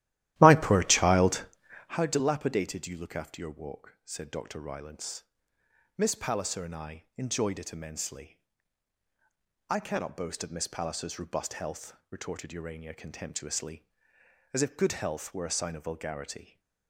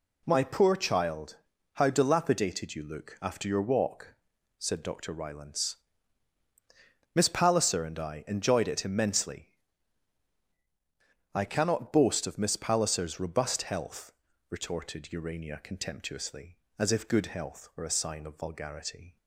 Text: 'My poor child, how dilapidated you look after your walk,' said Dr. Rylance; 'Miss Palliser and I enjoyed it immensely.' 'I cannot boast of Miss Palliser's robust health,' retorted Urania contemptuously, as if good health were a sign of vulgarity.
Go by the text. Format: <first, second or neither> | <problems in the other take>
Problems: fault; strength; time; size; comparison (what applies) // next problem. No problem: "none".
second | starts louder than the rest; strong; until 2.0 s; 14.5 dB